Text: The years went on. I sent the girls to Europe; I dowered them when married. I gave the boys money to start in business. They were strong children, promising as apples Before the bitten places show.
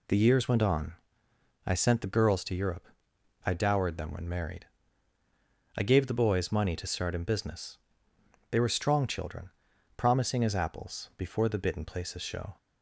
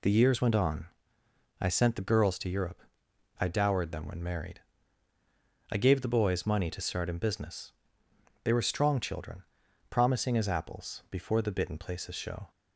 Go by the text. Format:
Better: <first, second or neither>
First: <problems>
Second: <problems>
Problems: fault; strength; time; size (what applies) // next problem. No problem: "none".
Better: neither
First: none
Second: none